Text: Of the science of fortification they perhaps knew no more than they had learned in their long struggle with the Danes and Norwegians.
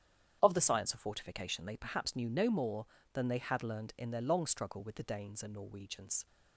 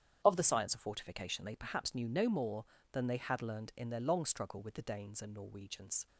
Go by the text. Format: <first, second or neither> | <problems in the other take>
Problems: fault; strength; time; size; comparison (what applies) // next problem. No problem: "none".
neither | starts louder than the rest; strong; the same in both